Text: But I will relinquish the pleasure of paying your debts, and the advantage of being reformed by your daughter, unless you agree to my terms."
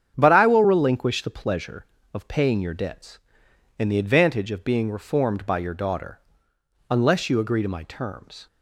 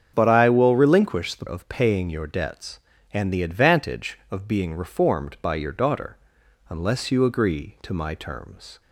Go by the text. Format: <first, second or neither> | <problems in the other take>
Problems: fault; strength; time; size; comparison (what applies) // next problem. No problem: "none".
first | starts louder than the rest; strong; until 1.1 s; 7.5 dB; strong in the first // skips "pleasure"; at 1.4 s